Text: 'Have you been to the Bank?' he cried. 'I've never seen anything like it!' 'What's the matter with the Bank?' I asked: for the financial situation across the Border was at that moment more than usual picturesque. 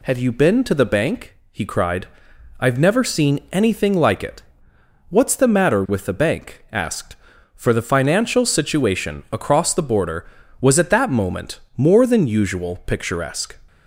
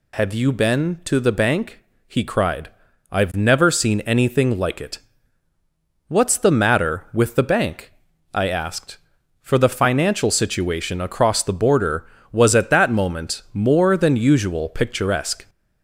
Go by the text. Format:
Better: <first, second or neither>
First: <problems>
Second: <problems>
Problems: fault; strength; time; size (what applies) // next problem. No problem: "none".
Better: second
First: skips "I"; at 6.6 s // pauses between "moment" and "more"; slight; at 11.5 s; 0.16 s long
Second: none